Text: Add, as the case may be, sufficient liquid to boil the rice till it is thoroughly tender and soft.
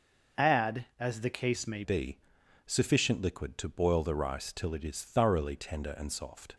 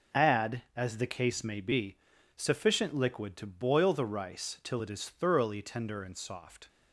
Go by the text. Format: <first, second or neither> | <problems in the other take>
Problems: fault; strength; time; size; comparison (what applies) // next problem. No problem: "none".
second | changes voice at "be"; from 1.8 s on; 4.7 s long